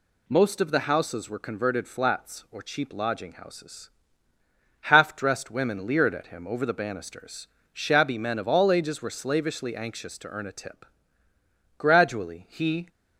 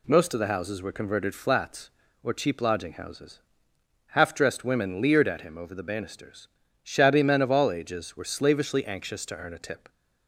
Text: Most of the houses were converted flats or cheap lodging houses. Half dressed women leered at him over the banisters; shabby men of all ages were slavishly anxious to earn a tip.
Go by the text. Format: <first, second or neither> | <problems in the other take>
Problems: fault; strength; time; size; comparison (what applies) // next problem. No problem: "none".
second | goes on to say "Gradually he"; noticeable; from 11.7 s on; 1.1 s long